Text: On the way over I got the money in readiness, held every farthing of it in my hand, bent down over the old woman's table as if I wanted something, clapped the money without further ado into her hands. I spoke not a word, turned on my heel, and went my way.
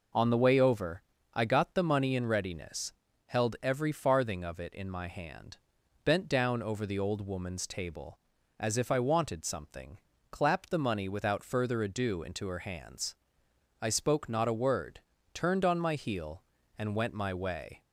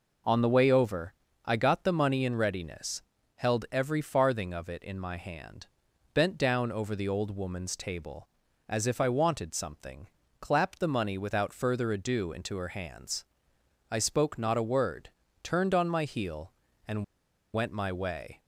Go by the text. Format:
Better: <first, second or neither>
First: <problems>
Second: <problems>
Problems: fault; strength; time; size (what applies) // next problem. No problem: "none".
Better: first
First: pauses between "over" and "I"; slight; at 1.0 s; 0.30 s long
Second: pauses between "over" and "I"; slight; at 1.1 s; 0.30 s long // pauses between "and" and "went"; noticeable; at 17.0 s; 0.49 s long